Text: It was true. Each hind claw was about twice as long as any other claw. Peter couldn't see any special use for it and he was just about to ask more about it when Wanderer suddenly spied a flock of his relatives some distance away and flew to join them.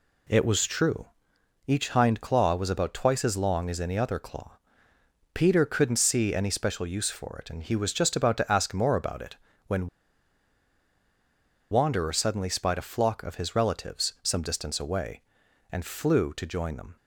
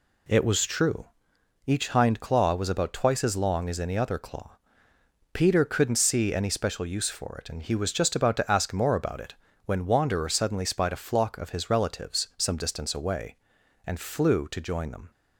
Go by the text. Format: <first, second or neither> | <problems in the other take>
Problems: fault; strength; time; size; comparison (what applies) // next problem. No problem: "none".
second | pauses between "it" and "when"; slight; at 9.3 s; 0.32 s long; slight in the second // pauses between "when" and "Wanderer"; strong; at 9.8 s; 1.8 s long